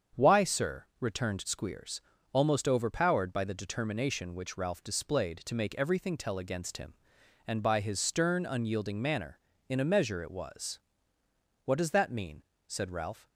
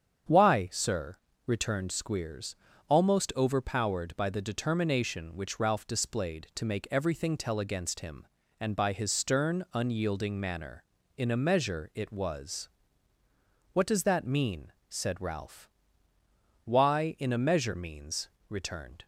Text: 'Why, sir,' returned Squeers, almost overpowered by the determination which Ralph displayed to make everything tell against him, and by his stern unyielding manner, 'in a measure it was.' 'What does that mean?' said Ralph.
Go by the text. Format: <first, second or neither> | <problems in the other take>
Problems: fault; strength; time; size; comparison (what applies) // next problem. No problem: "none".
first | starts louder than the rest; strong; until 1.6 s; 7.5 dB; strong in the first // goes on to say "Why in a measure means returned"; strong; from 16.6 s on; 2.4 s long